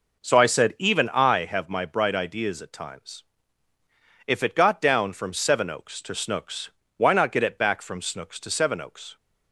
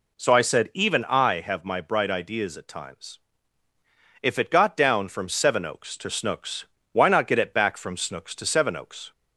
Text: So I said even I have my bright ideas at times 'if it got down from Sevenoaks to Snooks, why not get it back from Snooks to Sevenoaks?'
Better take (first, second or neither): second